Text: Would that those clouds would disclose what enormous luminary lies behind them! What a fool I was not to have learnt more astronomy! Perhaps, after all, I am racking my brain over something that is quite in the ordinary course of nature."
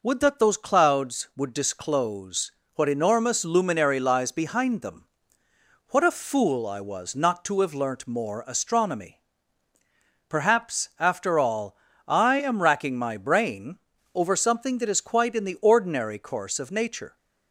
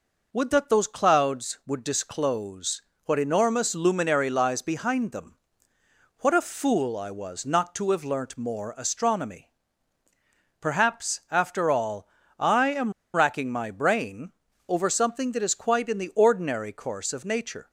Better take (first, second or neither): first